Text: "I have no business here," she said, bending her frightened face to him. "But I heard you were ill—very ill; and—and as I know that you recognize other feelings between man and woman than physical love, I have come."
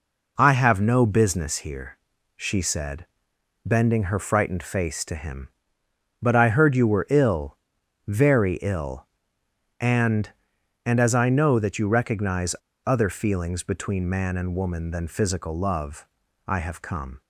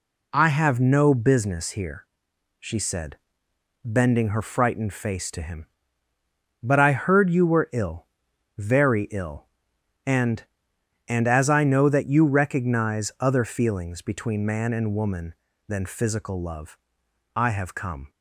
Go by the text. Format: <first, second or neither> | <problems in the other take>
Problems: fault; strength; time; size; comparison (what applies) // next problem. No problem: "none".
second | pauses between "recognize" and "other"; slight; at 12.5 s; 0.31 s long